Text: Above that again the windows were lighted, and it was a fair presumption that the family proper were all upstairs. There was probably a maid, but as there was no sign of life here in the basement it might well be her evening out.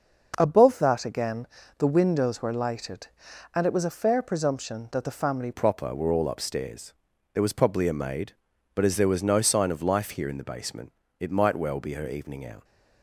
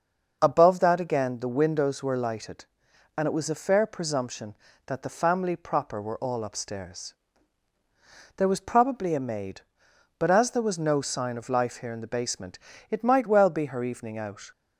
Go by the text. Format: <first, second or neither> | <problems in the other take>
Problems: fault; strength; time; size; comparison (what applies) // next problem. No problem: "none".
second | starts louder than the rest; until 1.3 s; 6 dB; also in the second // pauses between "again" and "the"; slight; at 1.4 s; 0.32 s long // changes voice at "proper"; from 5.5 s on; 7.1 s long // pauses between "basement" and "it"; slight; at 10.9 s; 0.28 s long; slight in the second